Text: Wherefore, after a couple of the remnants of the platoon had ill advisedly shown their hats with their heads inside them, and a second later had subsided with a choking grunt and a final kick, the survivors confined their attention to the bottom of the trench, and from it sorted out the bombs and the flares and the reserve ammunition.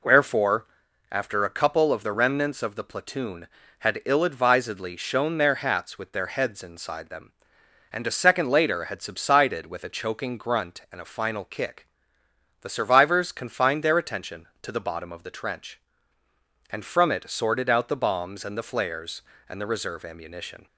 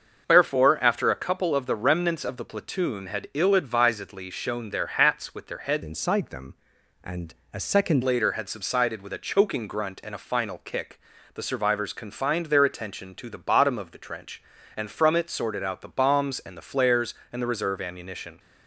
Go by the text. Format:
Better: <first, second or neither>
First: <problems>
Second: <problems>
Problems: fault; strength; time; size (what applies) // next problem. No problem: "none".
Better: first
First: none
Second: starts louder than the rest; until 1.2 s; 6 dB // changes voice from "inside" to "second"; from 5.8 to 8.0 s; 2.2 s long // pauses between "and" and "a"; slight; at 7.3 s; 0.20 s long